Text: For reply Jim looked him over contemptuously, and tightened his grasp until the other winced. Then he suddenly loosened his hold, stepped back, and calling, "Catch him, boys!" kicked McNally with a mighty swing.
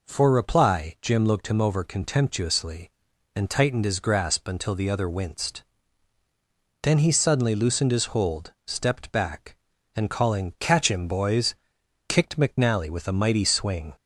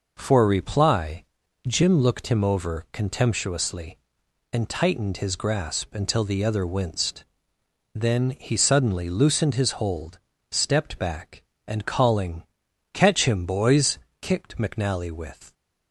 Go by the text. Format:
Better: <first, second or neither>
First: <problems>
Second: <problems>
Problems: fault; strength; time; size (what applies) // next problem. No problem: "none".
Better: first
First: none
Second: pauses between "reply" and "Jim"; at 1.2 s; 0.42 s long // stops before "a mighty swing"; at 15.5 s